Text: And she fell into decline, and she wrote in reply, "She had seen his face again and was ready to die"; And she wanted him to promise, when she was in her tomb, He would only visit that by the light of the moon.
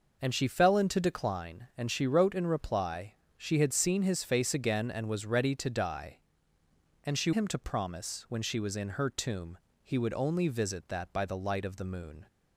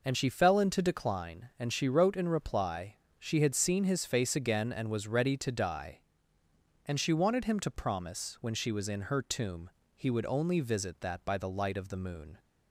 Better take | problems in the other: second | skips "wanted"; at 7.3 s

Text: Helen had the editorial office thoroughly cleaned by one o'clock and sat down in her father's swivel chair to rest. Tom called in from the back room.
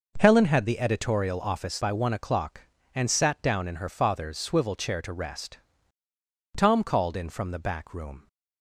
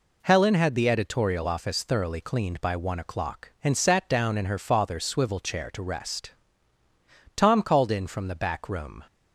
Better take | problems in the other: second | skips "thoroughly cleaned"; at 1.8 s

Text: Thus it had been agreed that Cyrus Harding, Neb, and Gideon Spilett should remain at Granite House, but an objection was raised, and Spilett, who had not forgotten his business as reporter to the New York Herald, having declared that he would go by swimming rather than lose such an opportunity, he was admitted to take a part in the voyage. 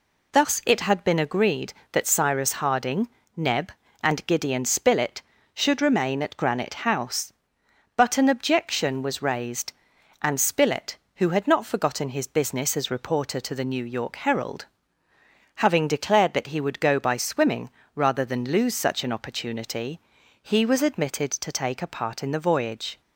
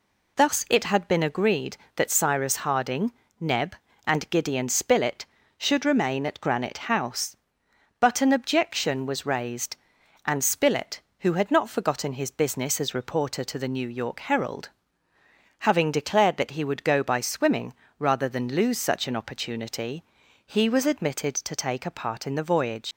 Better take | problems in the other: first | pauses between "swimming" and "rather"; slight; at 17.7 s; 0.26 s long; slight in the first // leaves "voyage" unfinished; at 22.9 s; 125 ms

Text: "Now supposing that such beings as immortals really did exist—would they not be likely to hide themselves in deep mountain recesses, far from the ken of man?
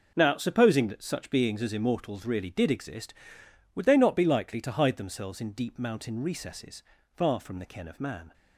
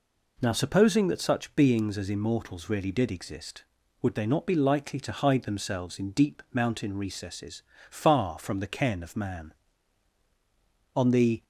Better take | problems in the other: first | goes on to say "On the"; slight; from 10.9 s on; 0.48 s long

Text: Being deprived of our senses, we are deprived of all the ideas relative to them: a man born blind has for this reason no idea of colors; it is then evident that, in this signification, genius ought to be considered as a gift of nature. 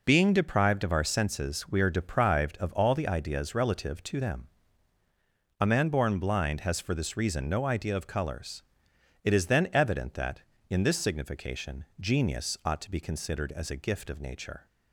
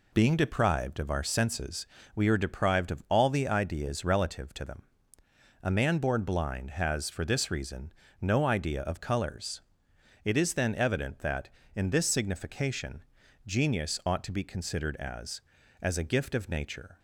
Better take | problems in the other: first | pauses between "reason" and "no"; slight; at 7.9 s; 0.30 s long // says "as" twice; at 15.8 s

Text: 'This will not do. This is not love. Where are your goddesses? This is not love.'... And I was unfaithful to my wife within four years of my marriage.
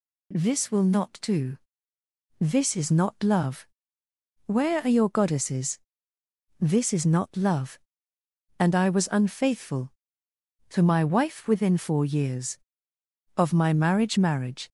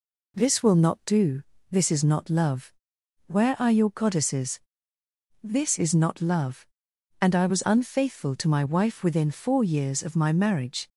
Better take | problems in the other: second | says "marriage" twice; at 14.1 s

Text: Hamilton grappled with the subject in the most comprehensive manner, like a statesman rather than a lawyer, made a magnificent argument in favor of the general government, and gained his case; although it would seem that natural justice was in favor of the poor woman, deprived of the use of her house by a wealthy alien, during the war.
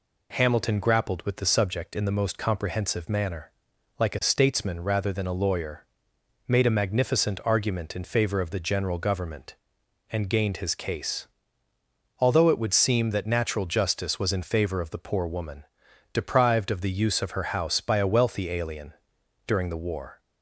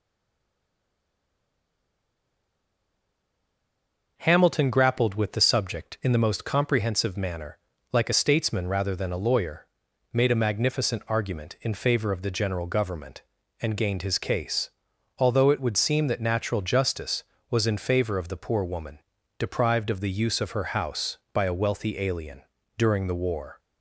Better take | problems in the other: first | stays silent before the first word; strong; until 4.1 s; 4.1 s long

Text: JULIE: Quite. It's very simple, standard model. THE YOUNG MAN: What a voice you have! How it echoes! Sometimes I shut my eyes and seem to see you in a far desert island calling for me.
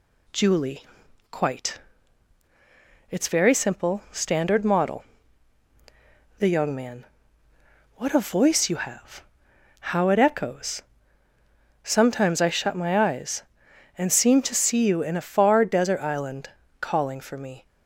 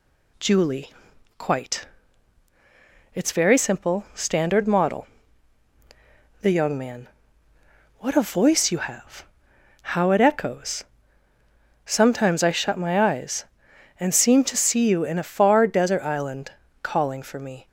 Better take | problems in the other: neither | pauses between "island" and "calling"; slight; the same in both

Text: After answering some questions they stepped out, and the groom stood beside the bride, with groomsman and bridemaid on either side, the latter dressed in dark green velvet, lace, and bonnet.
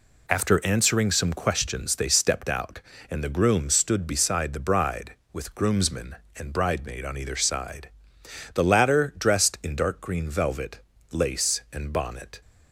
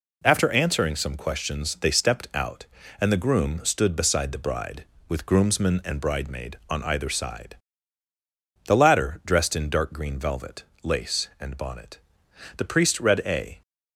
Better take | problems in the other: first | goes on to say "The priest read a"; noticeable; from 12.5 s on; 1.0 s long

